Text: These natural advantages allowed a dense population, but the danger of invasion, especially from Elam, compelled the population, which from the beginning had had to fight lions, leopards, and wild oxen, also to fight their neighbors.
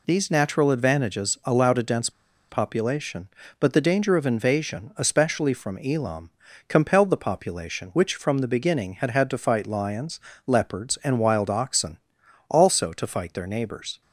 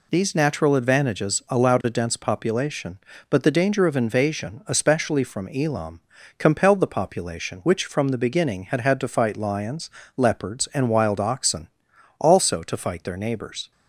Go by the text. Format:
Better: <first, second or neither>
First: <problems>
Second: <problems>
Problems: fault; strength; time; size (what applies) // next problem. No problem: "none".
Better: second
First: pauses between "dense" and "population"; at 2.0 s; 0.39 s long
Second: none